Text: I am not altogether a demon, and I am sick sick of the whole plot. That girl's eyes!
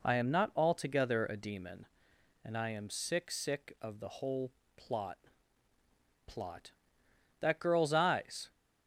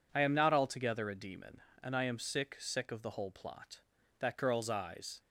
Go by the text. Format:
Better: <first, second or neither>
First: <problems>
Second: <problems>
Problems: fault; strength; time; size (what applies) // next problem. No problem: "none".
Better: second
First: pauses between "whole" and "plot"; slight; at 4.5 s; 0.24 s long // says "plot" twice; at 6.2 s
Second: none